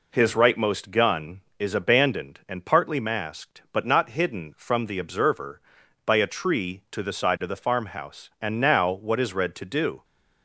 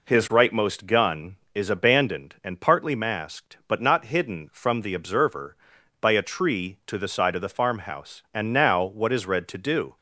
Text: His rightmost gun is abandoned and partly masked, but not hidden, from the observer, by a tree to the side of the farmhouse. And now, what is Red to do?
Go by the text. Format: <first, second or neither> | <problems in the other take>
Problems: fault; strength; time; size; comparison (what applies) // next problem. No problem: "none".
neither | none